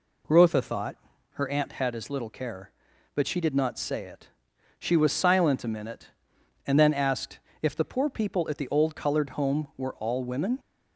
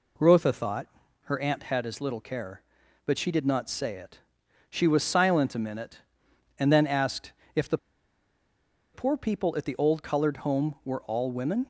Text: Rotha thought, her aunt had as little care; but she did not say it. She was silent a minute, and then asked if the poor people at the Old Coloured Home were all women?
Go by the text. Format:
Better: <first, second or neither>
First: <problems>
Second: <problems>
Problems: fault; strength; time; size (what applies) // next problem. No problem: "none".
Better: first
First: pauses between "asked" and "if"; slight; at 7.3 s; 0.22 s long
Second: pauses between "asked" and "if"; slight; at 7.3 s; 0.22 s long // pauses between "the" and "poor"; at 7.7 s; 1.1 s long